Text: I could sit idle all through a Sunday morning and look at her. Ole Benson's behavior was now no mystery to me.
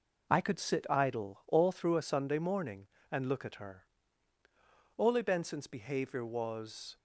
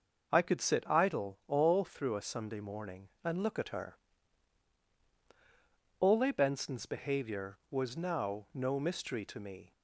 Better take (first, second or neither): second